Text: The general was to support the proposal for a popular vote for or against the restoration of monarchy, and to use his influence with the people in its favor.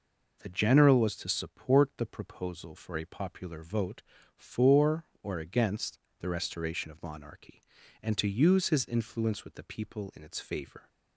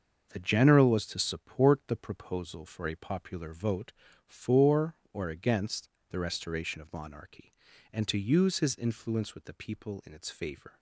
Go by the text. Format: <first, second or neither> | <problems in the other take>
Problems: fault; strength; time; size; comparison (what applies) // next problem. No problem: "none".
first | gets quieter; strong; throughout; 7 dB // pauses between "against" and "the"; slight; at 5.8 s; 0.22 s long; slight in the first